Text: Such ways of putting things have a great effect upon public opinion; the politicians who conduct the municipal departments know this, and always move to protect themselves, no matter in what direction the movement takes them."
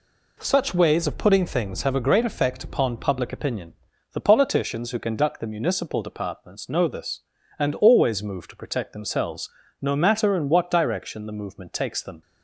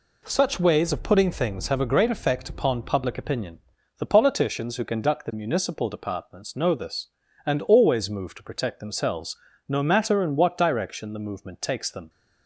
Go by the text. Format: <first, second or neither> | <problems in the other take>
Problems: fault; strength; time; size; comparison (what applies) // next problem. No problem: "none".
neither | none